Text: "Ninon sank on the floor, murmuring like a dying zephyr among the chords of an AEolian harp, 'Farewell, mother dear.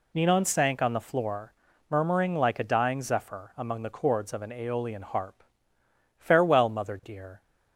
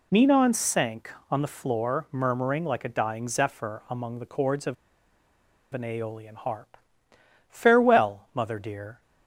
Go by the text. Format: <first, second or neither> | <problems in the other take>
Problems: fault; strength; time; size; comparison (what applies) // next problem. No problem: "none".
first | pauses between "of" and "an"; at 4.7 s; 0.99 s long